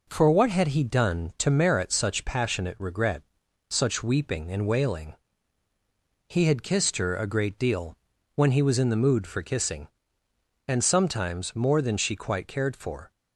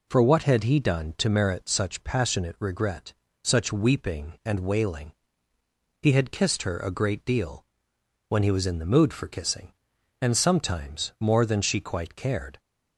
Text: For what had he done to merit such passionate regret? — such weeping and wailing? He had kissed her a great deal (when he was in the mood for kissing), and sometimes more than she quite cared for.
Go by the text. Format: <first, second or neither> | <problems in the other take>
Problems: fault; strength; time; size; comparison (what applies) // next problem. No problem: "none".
first | stops before "for"; at 12.5 s